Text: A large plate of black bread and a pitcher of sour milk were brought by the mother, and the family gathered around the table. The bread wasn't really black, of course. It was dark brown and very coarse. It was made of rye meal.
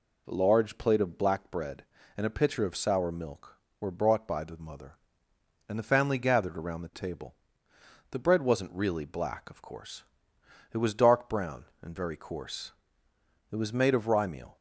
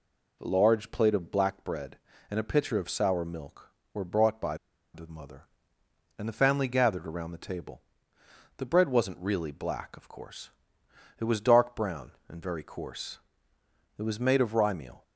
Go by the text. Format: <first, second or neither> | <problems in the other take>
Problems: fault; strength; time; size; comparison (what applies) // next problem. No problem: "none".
first | pauses between "by" and "the"; at 4.5 s; 0.37 s long